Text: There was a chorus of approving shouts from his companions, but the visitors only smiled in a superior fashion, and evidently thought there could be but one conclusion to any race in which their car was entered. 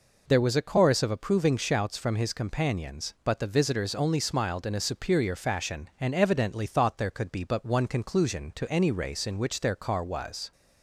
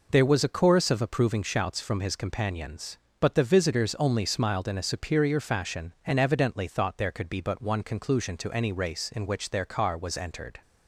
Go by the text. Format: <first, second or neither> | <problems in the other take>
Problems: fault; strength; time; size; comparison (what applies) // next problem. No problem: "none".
second | stops before "entered"; at 10.5 s